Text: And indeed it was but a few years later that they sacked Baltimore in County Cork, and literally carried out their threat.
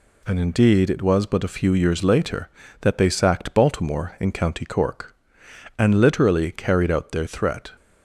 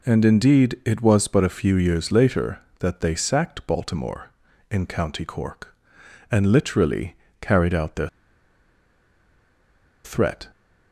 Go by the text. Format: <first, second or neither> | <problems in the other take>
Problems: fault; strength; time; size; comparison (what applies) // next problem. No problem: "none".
first | pauses between "literally" and "carried"; slight; at 7.1 s; 0.24 s long // pauses between "their" and "threat"; strong; at 8.0 s; 1.9 s long